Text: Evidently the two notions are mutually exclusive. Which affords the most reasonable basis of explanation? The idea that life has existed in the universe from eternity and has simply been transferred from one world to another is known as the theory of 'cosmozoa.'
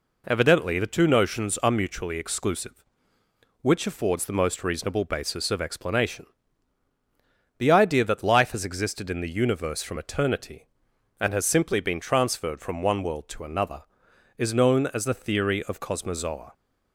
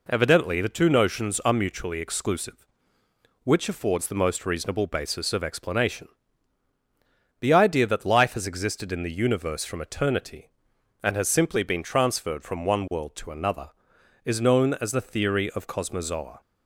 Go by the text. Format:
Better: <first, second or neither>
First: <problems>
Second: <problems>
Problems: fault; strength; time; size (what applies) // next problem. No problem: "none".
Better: neither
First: none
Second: none